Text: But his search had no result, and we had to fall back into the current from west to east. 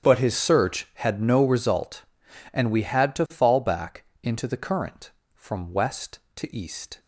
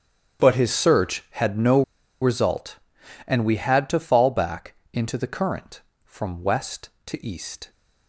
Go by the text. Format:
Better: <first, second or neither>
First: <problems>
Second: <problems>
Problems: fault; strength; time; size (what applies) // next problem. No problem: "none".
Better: first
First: starts louder than the rest; strong; until 1.1 s; 9 dB // pauses between "back" and "into"; slight; at 4.0 s; 0.18 s long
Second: starts louder than the rest; strong; until 1.5 s; 9 dB // pauses between "no" and "result"; at 1.8 s; 0.38 s long // pauses between "back" and "into"; slight; at 4.7 s; 0.18 s long